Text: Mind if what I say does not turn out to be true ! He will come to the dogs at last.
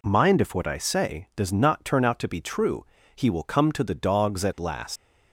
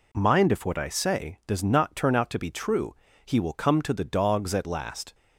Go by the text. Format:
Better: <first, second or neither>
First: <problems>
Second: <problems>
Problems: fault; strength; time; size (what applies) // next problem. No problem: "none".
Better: second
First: leaves "last" unfinished; at 4.9 s; 115 ms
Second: none